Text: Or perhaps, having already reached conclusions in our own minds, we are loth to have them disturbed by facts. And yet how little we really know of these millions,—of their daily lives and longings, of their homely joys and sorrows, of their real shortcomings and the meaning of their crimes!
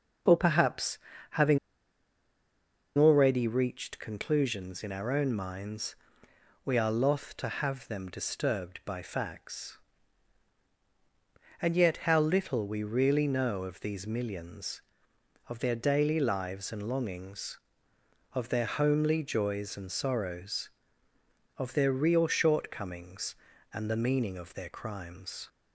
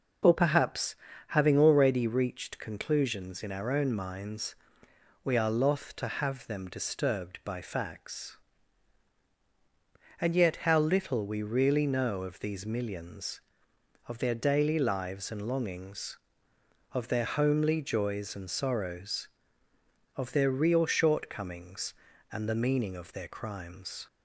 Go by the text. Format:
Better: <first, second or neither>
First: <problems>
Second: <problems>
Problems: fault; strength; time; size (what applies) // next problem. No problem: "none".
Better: second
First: pauses between "having" and "already"; strong; at 1.5 s; 1.3 s long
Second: none